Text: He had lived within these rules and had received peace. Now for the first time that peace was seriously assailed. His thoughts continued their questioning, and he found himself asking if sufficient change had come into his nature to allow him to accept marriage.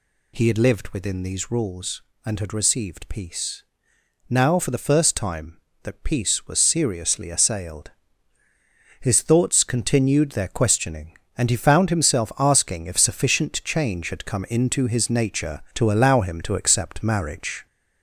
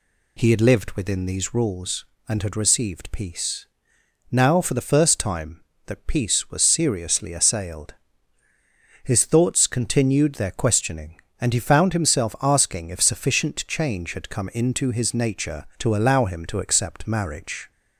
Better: second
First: gets louder; noticeable; throughout; 4 dB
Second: none

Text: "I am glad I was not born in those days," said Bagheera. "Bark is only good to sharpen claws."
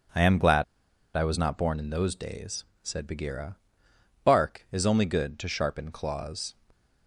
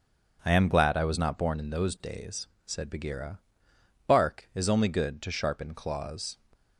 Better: second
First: starts louder than the rest; until 1.6 s; 7 dB // pauses between "glad" and "I"; noticeable; at 0.6 s; 0.51 s long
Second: none

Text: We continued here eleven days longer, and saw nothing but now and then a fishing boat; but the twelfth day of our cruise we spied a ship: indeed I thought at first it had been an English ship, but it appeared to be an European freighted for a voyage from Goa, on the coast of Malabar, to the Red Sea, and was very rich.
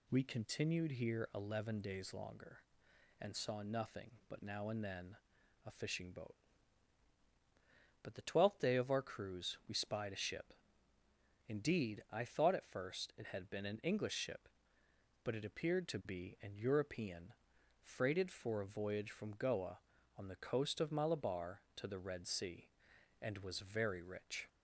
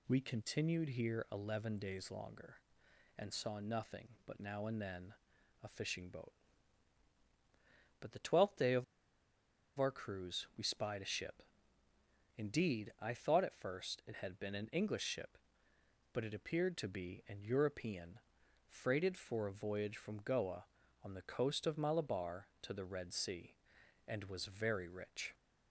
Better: first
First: pauses between "then" and "a"; noticeable; at 5.1 s; 0.48 s long // pauses between "European" and "freighted"; noticeable; at 17.3 s; 0.46 s long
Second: pauses between "then" and "a"; noticeable; at 5.1 s; 0.48 s long // pauses between "of" and "our"; noticeable; at 8.8 s; 0.93 s long // pauses between "European" and "freighted"; noticeable; at 18.1 s; 0.46 s long

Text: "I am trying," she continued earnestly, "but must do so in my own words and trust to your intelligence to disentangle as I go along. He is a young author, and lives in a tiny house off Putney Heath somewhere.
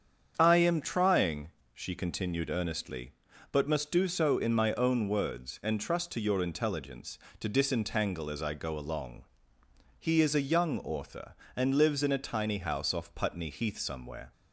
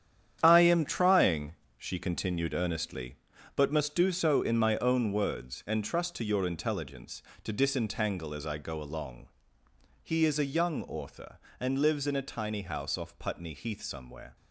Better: first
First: starts louder than the rest; strong; until 1.4 s; 7.5 dB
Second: gets quieter; strong; throughout; 10.5 dB // starts louder than the rest; strong; until 1.4 s; 9.5 dB

